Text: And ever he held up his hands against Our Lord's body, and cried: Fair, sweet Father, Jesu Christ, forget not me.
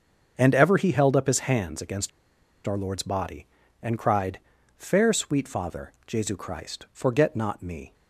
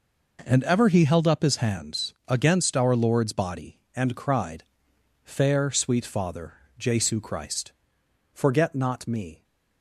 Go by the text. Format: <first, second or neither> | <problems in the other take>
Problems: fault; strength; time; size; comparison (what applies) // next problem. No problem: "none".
second | starts louder than the rest; until 1.3 s; 7 dB // pauses between "against" and "Our"; noticeable; at 2.0 s; 0.56 s long